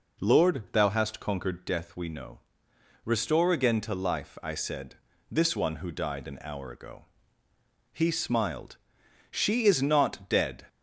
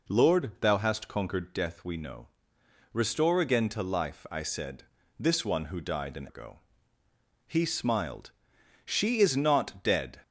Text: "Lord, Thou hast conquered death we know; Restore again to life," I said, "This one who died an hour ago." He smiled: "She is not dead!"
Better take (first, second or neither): first